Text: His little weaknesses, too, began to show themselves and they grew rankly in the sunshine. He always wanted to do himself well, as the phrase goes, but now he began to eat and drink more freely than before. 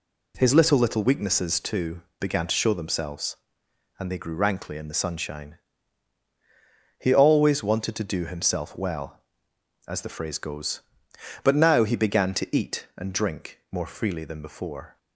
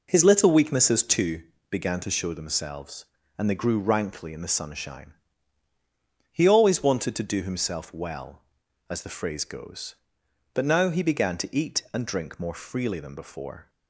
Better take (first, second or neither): second